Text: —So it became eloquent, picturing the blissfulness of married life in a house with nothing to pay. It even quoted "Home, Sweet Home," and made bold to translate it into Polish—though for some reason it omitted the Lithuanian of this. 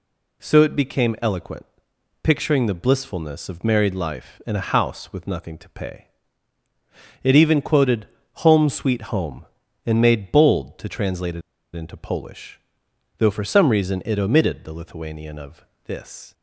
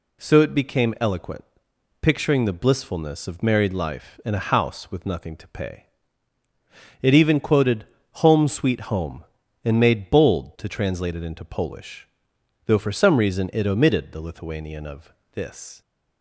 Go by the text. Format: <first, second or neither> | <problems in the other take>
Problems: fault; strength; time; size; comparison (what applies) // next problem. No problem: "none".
second | pauses between "quoted" and "Home"; slight; at 8.0 s; 0.34 s long; slight in the second // pauses between "it" and "into"; slight; at 11.4 s; 0.33 s long // pauses between "of" and "this"; slight; at 15.6 s; 0.22 s long; slight in the second